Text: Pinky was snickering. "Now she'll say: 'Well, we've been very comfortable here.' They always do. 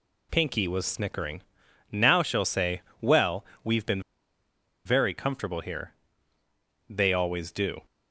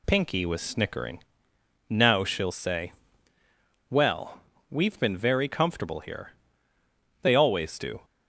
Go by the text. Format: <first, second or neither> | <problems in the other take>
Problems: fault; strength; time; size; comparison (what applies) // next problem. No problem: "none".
second | pauses between "been" and "very"; noticeable; at 4.0 s; 0.85 s long